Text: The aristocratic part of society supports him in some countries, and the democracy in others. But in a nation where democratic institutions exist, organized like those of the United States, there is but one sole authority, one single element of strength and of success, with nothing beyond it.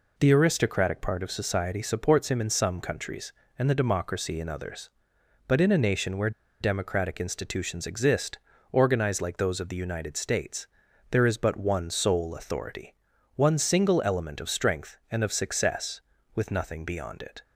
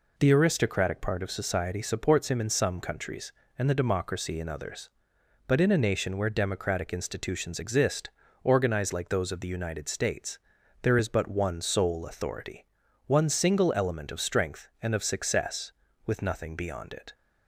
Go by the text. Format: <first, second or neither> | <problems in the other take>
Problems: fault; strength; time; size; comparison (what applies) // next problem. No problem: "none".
second | pauses between "where" and "democratic"; slight; at 6.3 s; 0.30 s long